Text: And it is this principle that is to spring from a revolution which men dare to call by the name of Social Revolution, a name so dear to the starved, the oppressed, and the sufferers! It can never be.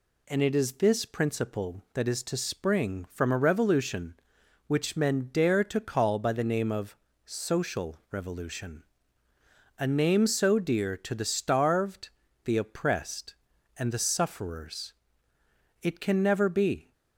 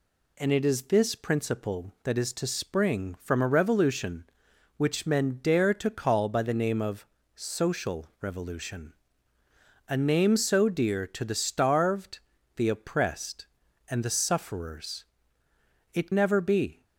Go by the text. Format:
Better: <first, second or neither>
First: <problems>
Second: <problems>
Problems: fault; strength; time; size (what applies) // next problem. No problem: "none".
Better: first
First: pauses between "of" and "Social"; slight; at 6.9 s; 0.30 s long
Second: pauses between "of" and "Social"; slight; at 7.0 s; 0.30 s long // skips "can"; at 16.1 s